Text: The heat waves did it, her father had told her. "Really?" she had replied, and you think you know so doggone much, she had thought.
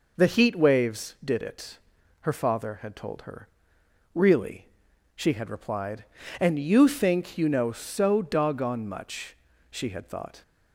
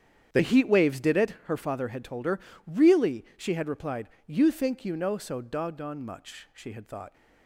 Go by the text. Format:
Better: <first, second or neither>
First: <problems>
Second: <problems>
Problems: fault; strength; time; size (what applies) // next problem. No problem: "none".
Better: first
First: none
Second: starts louder than the rest; strong; until 1.4 s; 8.5 dB // skips "and"; at 4.1 s